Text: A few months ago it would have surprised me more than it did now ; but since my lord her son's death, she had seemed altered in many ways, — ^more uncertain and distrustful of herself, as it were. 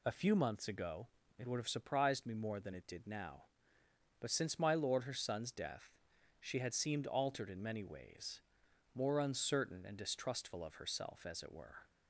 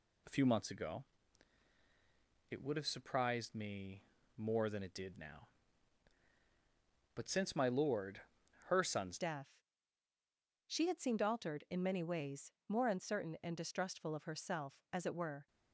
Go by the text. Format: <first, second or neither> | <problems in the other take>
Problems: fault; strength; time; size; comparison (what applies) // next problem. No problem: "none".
first | pauses between "ago" and "it"; strong; at 1.0 s; 1.4 s long; slight in the first // pauses between "me" and "more"; slight; at 4.0 s; 0.34 s long // pauses between "lord" and "her"; noticeable; at 8.2 s; 0.46 s long // changes voice at "death"; from 9.1 s on; 6.3 s long